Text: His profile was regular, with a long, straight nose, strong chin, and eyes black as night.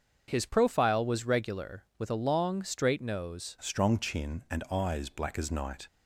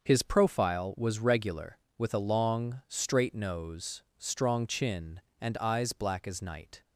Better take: second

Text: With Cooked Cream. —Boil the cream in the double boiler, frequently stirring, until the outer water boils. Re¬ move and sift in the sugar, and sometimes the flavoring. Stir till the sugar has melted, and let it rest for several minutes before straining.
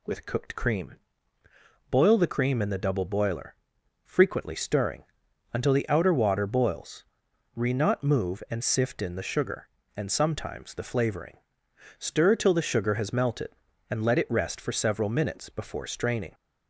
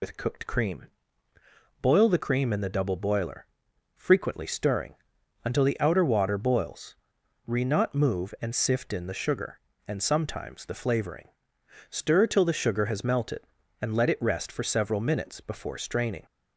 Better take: first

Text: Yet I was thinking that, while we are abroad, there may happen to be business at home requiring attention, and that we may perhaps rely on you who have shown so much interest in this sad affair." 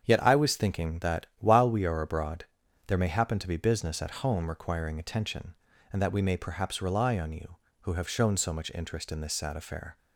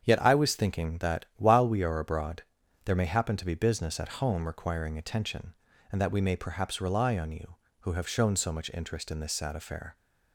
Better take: neither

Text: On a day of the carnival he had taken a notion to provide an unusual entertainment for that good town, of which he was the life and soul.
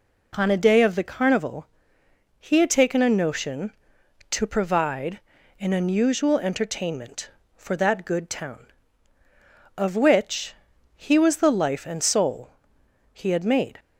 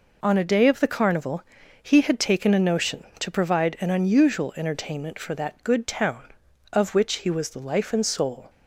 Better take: second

